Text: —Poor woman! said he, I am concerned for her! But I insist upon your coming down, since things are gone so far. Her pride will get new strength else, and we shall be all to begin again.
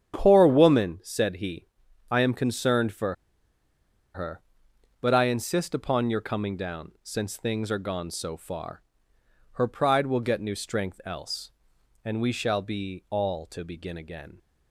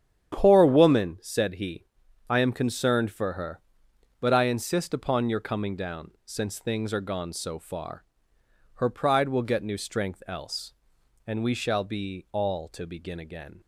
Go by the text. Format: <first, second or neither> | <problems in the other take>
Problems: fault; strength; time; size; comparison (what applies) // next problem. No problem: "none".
second | starts louder than the rest; strong; until 1.1 s; 9 dB; strong in the second // pauses between "for" and "her"; at 3.1 s; 0.99 s long